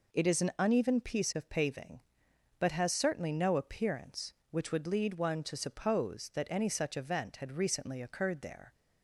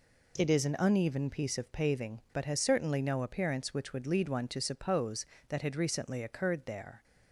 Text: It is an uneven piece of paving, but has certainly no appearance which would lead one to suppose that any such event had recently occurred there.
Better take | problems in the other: first | skips "any such event"; at 5.6 s

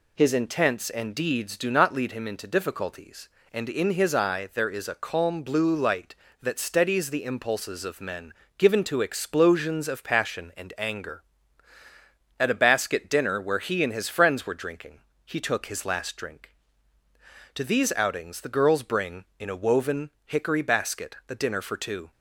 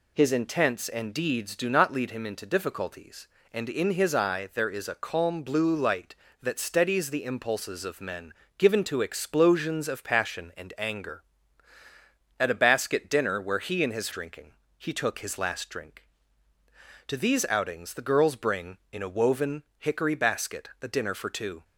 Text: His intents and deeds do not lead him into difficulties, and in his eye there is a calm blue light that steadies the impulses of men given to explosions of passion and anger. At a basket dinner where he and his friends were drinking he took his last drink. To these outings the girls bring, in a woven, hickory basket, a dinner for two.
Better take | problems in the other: first | pauses between "men" and "given"; slight; at 8.3 s; 0.26 s long; slight in the first // skips "friends were"; at 14.0 s // pauses between "drinking" and "he"; slight; at 14.5 s; 0.28 s long; slight in the first

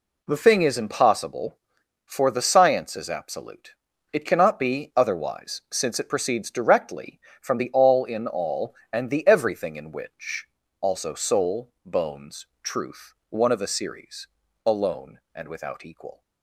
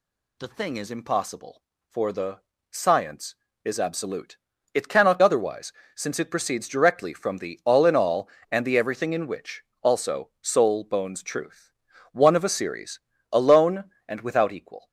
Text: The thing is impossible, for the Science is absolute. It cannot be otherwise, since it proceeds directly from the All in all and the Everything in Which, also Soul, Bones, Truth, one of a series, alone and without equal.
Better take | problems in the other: first | pauses between "the" and "Science"; slight; at 2.3 s; 0.30 s long // skips "be"; at 5.1 s

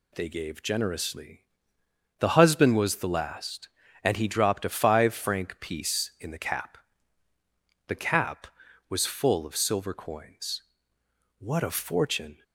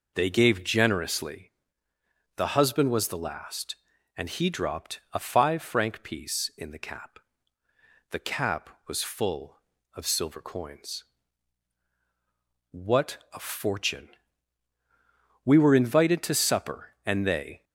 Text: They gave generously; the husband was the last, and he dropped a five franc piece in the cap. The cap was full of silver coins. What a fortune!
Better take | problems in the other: first | pauses between "What" and "a"; slight; at 13.1 s; 0.16 s long // goes on to say "We were invited to supper and they"; strong; from 15.4 s on; 2.2 s long

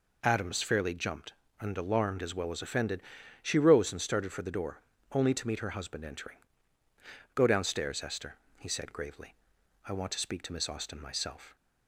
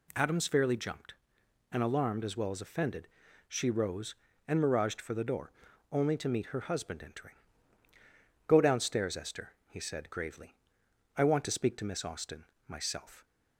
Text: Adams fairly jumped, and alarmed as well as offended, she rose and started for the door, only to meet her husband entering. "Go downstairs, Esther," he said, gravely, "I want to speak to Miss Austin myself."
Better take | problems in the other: first | says "miraged" for "started"; at 4.6 s // pauses between "Austin" and "myself"; slight; at 12.4 s; 0.20 s long

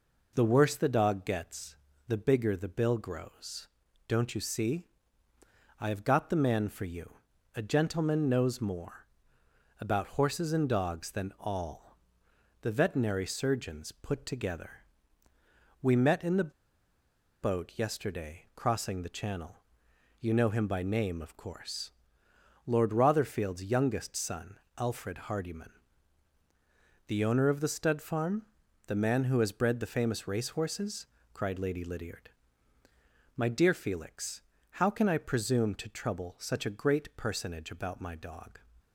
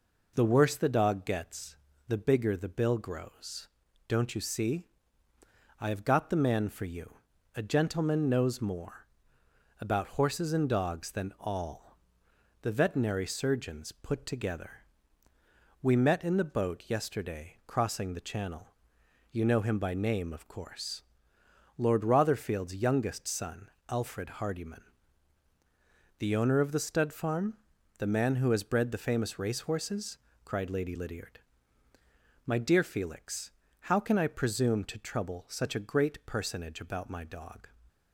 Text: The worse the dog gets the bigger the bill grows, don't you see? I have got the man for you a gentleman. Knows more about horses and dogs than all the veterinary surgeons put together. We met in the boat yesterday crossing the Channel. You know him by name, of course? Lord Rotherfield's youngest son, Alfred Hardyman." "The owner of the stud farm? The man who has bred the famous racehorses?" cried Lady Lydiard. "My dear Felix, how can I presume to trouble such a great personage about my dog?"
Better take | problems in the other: second | pauses between "gets" and "the"; slight; at 1.7 s; 0.32 s long; slight in the second // pauses between "you" and "a"; at 7.1 s; 0.42 s long; also in the second // pauses between "more" and "about"; noticeable; at 9.0 s; 0.74 s long; noticeable in the second // pauses between "all" and "the"; noticeable; at 11.9 s; 0.64 s long; noticeable in the second // pauses between "the" and "boat"; noticeable; at 16.5 s; 0.91 s long

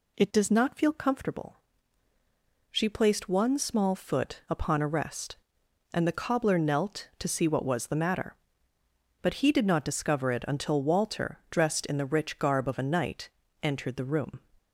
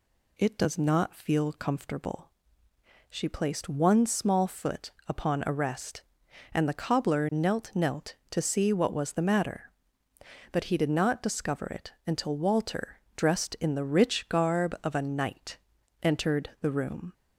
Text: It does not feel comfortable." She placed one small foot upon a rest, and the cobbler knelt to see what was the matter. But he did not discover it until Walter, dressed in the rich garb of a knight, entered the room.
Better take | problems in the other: first | pauses between "foot" and "upon"; slight; at 4.9 s; 0.16 s long // says "knelt" twice; at 7.7 s

